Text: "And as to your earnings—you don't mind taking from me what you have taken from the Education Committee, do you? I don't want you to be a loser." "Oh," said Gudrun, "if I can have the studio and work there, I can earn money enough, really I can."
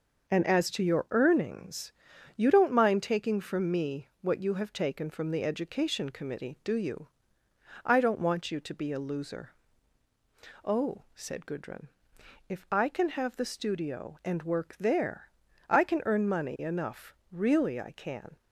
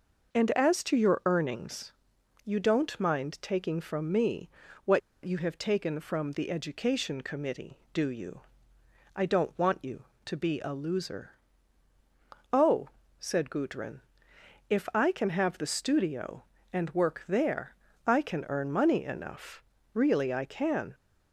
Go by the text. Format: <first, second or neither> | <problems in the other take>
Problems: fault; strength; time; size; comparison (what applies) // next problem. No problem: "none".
first | pauses between "me" and "what"; slight; at 4.4 s; 0.36 s long // pauses between "what" and "you"; slight; at 5.0 s; 0.25 s long